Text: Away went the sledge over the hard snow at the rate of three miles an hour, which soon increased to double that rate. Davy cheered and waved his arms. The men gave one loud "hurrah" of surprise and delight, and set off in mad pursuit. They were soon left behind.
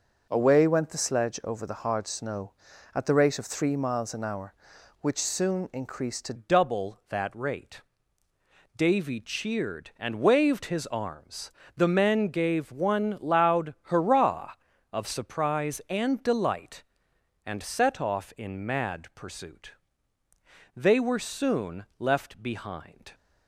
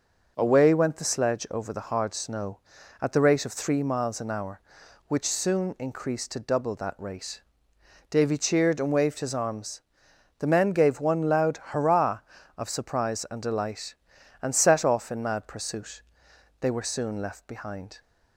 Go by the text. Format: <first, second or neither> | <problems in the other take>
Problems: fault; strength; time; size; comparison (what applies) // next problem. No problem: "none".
second | changes voice at "double"; from 6.3 s on; 16.8 s long